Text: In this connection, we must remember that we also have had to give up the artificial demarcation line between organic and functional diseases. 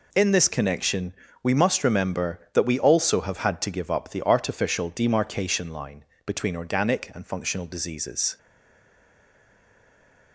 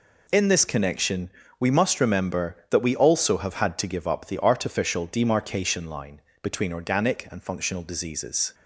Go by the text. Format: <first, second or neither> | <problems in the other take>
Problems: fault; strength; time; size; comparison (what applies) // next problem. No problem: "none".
second | pauses between "line" and "between"; slight; at 6.0 s; 0.22 s long; slight in the second // stays silent after the last word; noticeable; from 8.3 s on; 2.0 s long